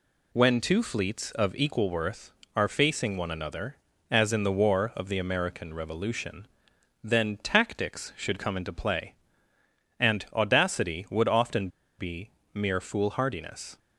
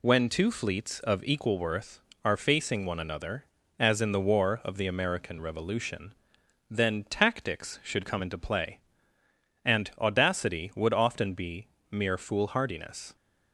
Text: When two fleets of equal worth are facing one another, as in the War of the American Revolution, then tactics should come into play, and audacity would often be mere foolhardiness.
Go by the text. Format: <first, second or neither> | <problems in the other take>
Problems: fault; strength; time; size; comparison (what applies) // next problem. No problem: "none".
second | pauses between "often" and "be"; slight; at 11.6 s; 0.31 s long // pauses between "be" and "mere"; slight; at 12.2 s; 0.24 s long; slight in the second